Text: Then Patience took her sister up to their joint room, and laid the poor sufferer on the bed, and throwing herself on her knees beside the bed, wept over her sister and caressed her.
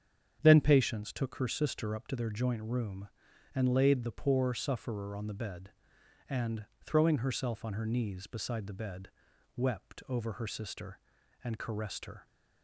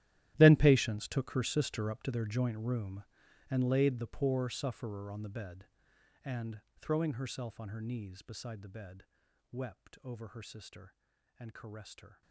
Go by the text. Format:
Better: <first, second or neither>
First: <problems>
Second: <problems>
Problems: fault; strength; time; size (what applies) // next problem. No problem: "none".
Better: first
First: starts louder than the rest; strong; until 1.4 s; 8 dB // pauses between "and" and "throwing"; slight; at 6.6 s; 0.18 s long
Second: gets quieter; strong; throughout; 18.5 dB // starts louder than the rest; strong; until 1.3 s; 13.5 dB // pauses between "and" and "throwing"; slight; at 6.5 s; 0.18 s long